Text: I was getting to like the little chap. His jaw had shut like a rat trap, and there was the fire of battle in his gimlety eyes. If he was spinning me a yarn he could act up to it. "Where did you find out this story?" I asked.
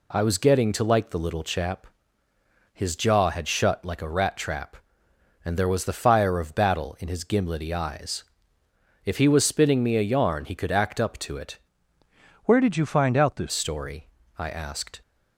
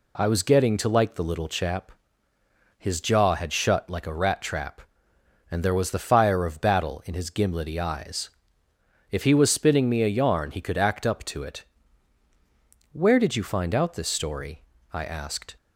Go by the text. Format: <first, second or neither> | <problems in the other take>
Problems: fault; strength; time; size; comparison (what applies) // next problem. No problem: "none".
second | changes voice from "Where" to "this"; from 12.4 to 13.5 s; 1.1 s long